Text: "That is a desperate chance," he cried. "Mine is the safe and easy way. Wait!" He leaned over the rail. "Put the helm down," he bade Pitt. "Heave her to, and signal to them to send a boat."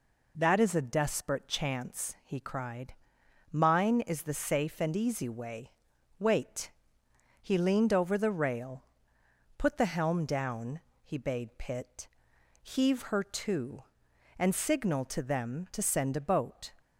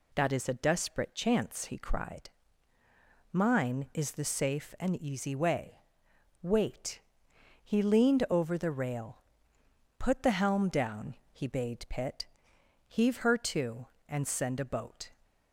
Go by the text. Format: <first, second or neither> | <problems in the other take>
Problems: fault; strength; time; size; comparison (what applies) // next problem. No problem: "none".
first | skips "signal to them to"; at 14.2 s